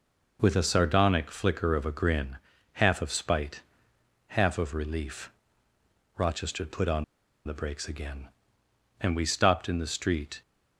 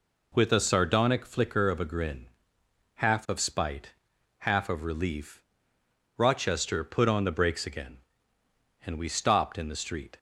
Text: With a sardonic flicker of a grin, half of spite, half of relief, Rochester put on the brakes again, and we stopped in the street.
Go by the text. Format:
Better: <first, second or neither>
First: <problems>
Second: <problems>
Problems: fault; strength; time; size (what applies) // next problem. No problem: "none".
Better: second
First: pauses between "on" and "the"; at 7.0 s; 0.41 s long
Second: none